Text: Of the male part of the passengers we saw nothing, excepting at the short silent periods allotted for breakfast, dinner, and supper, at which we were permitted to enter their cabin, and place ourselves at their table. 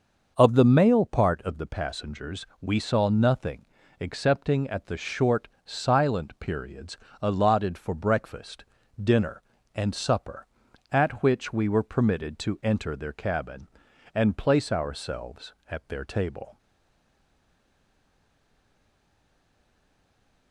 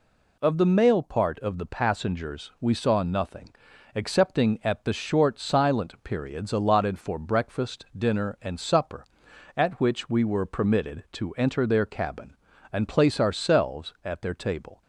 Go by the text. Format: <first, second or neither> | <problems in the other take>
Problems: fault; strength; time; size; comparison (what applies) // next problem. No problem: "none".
second | starts louder than the rest; noticeable; until 1.3 s; 6 dB // pauses between "passengers" and "we"; slight; at 2.4 s; 0.16 s long // pauses between "short" and "silent"; slight; at 5.4 s; 0.18 s long // pauses between "periods" and "allotted"; slight; at 6.9 s; 0.26 s long // stays silent after the last word; strong; from 16.5 s on; 4.0 s long